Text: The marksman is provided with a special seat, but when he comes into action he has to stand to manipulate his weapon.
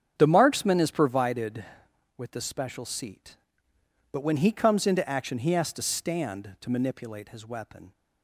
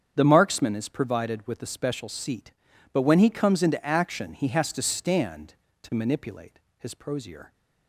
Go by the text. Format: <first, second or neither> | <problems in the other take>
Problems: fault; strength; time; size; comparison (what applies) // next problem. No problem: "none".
first | starts louder than the rest; strong; until 1.1 s; 8 dB; strong in the first // pauses between "manipulate" and "his"; slight; at 6.5 s; 0.20 s long // says "prosier" for "weapon"; at 6.9 s